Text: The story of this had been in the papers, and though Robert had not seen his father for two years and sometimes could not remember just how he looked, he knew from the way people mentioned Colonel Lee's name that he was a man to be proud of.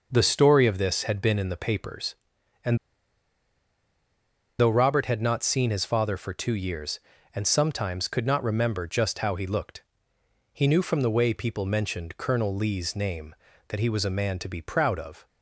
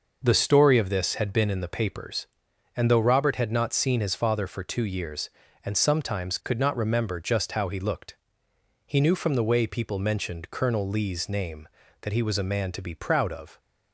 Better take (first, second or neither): second